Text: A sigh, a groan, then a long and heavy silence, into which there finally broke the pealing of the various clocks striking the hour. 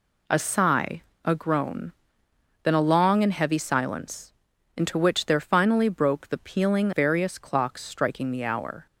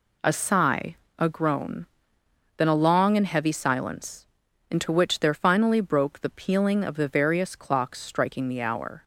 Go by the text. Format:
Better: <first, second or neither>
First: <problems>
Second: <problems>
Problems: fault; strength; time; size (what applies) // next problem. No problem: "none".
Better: second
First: skips "of the"; at 6.9 s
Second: none